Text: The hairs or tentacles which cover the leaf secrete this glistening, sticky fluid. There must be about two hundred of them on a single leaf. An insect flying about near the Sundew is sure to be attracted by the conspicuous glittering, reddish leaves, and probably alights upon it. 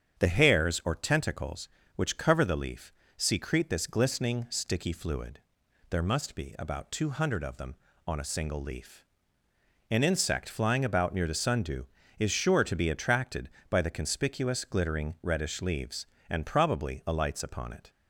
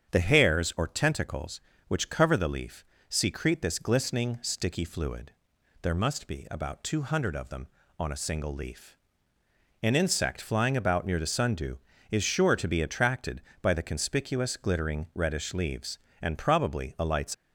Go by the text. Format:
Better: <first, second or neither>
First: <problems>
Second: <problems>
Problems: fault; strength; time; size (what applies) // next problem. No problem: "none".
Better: first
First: starts louder than the rest; strong; until 1.2 s; 8 dB // pauses between "leaf" and "secrete"; slight; at 2.9 s; 0.28 s long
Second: starts louder than the rest; strong; until 1.1 s; 8 dB // pauses between "leaf" and "secrete"; slight; at 2.8 s; 0.28 s long // stops before "upon it"; at 17.3 s